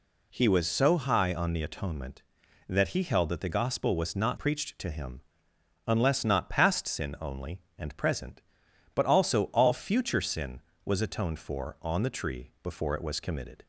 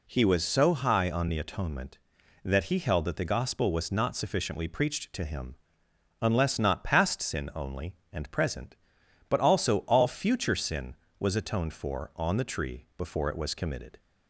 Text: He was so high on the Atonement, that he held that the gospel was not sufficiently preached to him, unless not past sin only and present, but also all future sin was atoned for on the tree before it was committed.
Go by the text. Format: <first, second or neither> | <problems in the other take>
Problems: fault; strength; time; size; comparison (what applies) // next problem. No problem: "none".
second | skips "sufficiently"; at 4.3 s